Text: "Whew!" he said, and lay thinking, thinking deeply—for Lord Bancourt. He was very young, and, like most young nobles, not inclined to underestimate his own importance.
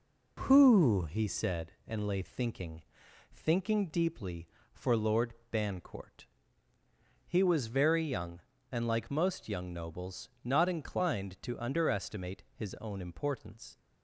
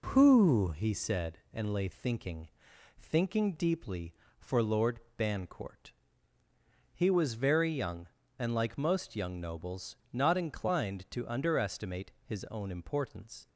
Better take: neither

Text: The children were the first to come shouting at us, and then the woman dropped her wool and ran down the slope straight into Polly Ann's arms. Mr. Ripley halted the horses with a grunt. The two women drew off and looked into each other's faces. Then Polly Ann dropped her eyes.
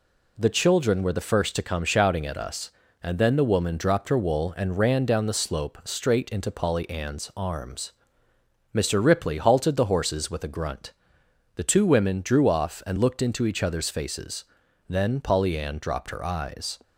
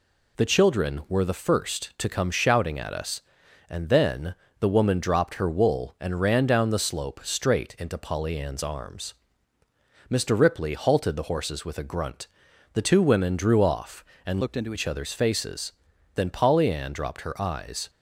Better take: first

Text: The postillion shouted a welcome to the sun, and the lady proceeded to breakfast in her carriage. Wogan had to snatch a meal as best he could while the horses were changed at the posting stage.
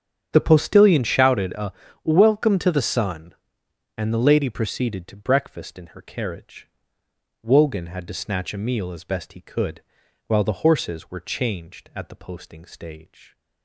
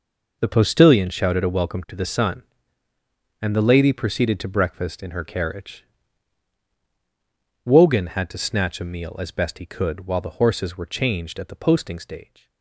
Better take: second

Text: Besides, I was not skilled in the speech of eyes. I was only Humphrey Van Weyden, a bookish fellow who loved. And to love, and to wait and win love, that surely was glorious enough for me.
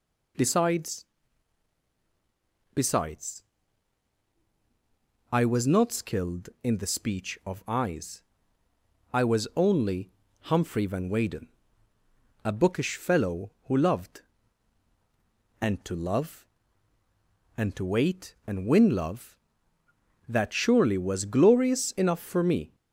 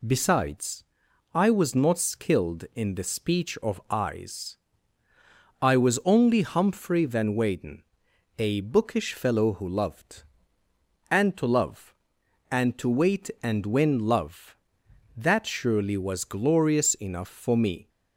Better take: second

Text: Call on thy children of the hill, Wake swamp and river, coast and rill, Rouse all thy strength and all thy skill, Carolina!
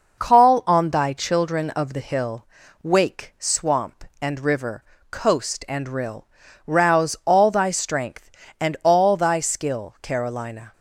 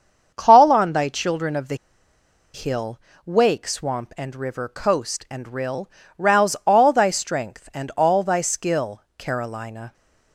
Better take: first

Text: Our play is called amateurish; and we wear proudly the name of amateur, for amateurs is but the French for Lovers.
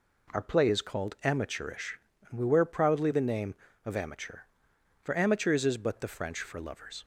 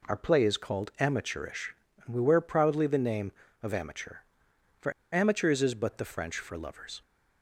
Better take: first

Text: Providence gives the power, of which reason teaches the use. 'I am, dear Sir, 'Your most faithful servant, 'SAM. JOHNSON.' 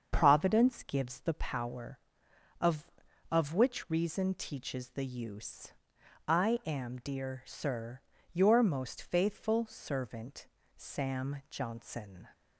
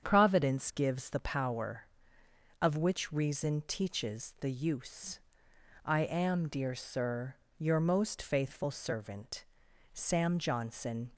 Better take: second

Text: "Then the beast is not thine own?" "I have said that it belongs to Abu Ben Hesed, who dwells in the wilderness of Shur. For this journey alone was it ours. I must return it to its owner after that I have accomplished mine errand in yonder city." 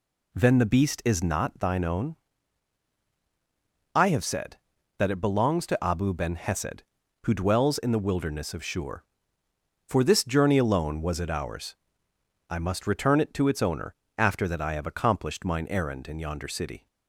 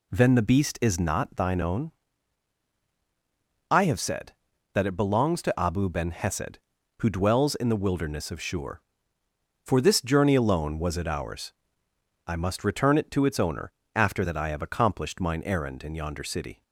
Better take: neither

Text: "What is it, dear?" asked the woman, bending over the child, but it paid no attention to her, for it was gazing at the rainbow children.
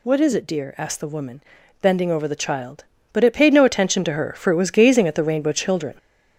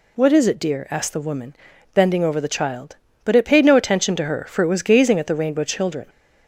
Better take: second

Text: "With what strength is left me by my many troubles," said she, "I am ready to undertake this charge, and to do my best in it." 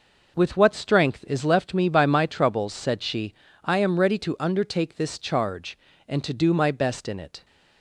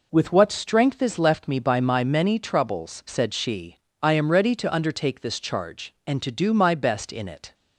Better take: second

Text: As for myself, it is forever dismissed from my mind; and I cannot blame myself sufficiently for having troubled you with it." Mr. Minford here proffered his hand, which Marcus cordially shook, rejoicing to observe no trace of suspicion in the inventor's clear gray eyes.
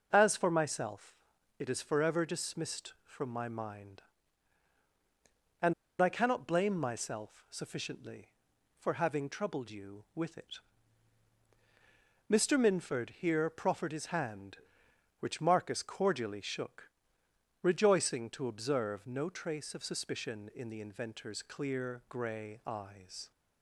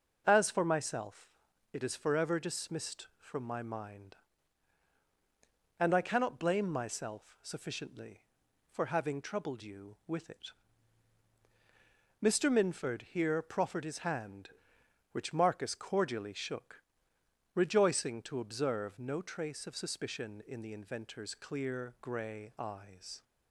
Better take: second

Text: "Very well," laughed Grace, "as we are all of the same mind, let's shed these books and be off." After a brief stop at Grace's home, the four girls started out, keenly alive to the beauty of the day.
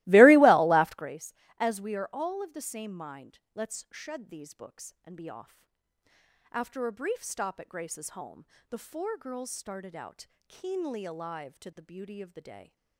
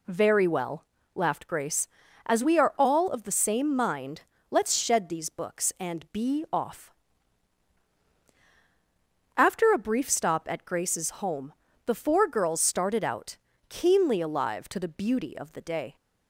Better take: second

